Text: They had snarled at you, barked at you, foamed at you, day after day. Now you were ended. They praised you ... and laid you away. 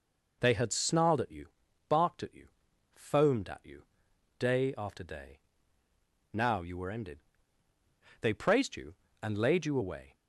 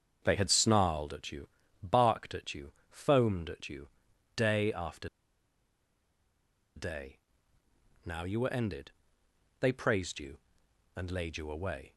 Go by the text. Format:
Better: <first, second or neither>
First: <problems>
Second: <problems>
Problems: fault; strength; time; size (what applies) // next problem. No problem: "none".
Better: first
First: none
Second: starts louder than the rest; strong; until 1.2 s; 7 dB // pauses between "after" and "day"; strong; at 5.0 s; 1.6 s long